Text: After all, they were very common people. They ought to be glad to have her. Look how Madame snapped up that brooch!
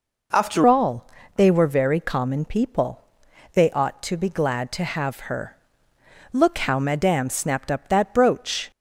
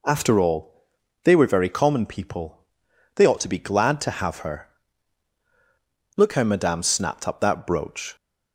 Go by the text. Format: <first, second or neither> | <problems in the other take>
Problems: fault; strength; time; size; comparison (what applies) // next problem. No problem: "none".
second | changes voice at "all"; from 0.6 s on; 8.1 s long